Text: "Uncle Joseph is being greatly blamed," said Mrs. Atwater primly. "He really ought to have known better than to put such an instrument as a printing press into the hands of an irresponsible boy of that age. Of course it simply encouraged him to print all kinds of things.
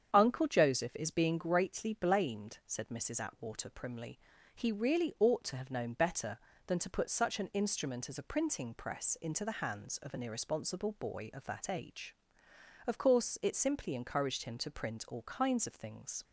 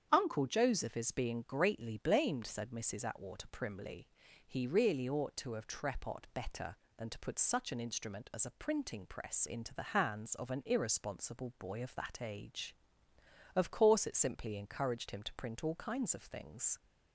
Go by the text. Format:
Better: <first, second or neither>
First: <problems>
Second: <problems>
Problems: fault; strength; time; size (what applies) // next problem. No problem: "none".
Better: first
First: starts louder than the rest; strong; until 1.1 s; 8 dB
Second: starts louder than the rest; strong; until 1.1 s; 8.5 dB // says "trepot" for "known"; at 5.6 s